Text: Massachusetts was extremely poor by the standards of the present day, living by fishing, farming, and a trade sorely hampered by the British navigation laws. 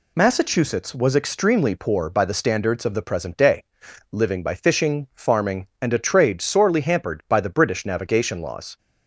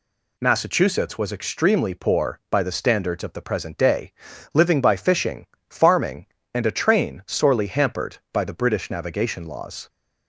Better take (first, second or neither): first